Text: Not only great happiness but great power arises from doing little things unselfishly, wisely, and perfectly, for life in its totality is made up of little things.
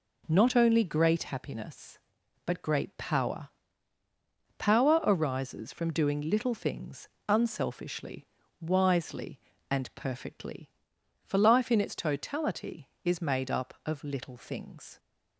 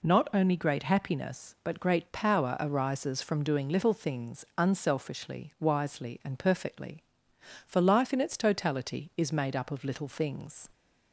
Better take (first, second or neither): second